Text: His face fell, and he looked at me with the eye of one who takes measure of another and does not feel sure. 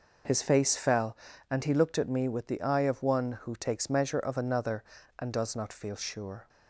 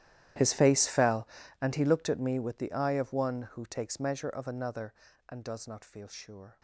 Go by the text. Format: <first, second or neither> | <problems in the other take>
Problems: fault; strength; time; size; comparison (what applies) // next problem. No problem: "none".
first | gets quieter; strong; throughout; 21 dB